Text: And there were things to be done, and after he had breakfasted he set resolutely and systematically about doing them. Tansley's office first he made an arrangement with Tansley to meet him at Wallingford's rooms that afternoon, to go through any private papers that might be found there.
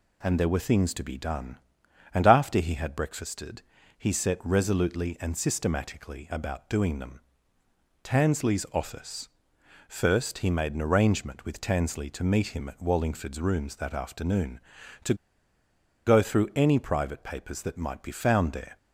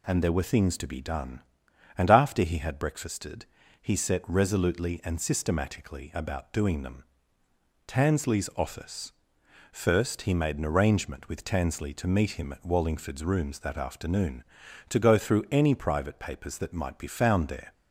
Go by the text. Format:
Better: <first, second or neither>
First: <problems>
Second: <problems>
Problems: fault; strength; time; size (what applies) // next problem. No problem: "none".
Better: second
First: pauses between "breakfasted" and "he"; slight; at 3.6 s; 0.36 s long // pauses between "office" and "first"; noticeable; at 9.2 s; 0.58 s long // pauses between "to" and "go"; noticeable; at 15.1 s; 0.91 s long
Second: pauses between "breakfasted" and "he"; slight; at 3.4 s; 0.36 s long // pauses between "office" and "first"; noticeable; at 9.1 s; 0.58 s long